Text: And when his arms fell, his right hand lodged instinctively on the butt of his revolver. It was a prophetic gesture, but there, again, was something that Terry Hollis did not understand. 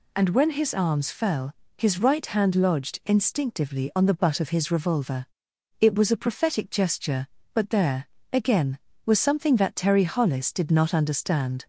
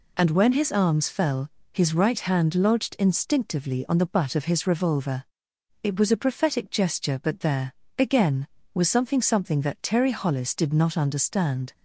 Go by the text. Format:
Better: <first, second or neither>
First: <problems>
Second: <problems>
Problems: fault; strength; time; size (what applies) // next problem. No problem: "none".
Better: first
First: none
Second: says "something" twice; at 9.2 s